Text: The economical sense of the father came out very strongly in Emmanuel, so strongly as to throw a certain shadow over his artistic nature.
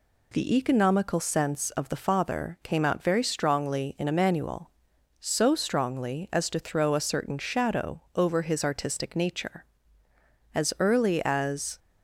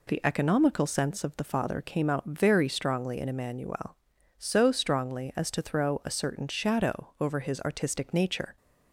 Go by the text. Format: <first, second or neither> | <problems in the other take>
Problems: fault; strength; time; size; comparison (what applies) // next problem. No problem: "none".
second | goes on to say "As early as"; noticeable; from 10.5 s on; 1.2 s long